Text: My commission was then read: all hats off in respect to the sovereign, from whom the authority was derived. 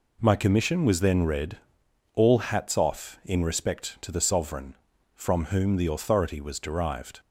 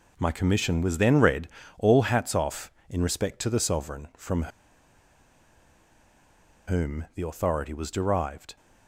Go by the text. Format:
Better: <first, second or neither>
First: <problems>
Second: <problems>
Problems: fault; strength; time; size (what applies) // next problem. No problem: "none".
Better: first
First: none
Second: pauses between "from" and "whom"; strong; at 4.4 s; 2.2 s long